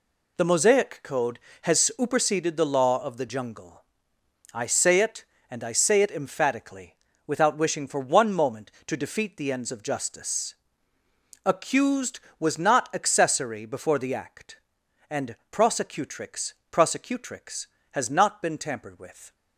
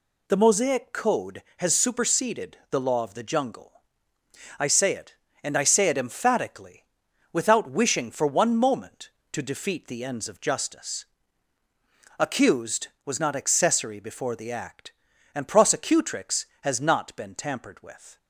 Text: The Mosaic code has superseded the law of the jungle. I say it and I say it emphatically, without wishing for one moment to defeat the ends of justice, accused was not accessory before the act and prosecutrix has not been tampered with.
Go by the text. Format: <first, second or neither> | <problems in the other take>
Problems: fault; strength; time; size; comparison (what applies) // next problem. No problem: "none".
second | pauses between "and" and "prosecutrix"; slight; at 15.3 s; 0.16 s long // says "prosecutrix" twice; at 16.7 s